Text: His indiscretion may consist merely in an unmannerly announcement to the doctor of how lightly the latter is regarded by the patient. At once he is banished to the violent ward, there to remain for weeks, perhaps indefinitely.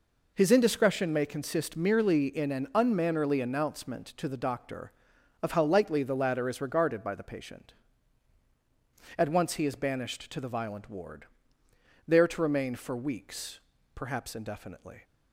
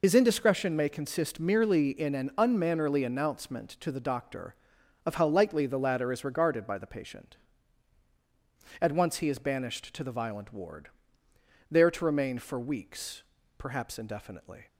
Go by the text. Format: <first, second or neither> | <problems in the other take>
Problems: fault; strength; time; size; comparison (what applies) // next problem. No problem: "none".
first | loses the start of "His"; at 0.0 s; 50 ms